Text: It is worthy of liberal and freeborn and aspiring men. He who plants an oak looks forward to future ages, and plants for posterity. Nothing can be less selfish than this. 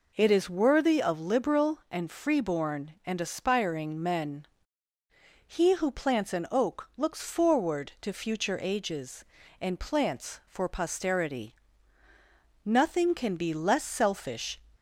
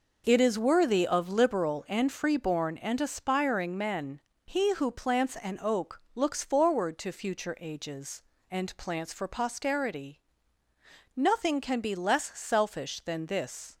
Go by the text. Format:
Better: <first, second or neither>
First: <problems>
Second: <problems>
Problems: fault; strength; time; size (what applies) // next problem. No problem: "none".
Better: second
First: stops before "than this"; at 14.7 s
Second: none